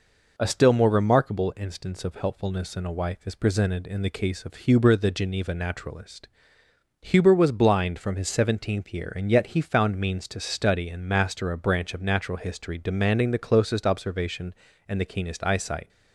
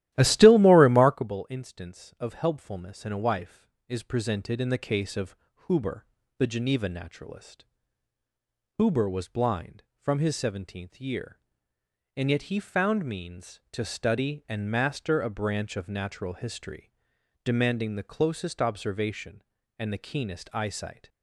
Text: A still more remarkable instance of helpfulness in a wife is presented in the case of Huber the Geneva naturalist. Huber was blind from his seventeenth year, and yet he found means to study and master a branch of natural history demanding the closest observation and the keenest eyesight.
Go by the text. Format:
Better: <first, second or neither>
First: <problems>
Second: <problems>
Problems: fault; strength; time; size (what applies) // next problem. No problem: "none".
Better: first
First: none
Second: starts louder than the rest; strong; until 1.3 s; 13.5 dB // pauses between "of" and "Huber"; slight; at 5.3 s; 0.32 s long // pauses between "Huber" and "the"; slight; at 6.0 s; 0.32 s long // pauses between "history" and "demanding"; noticeable; at 16.9 s; 0.52 s long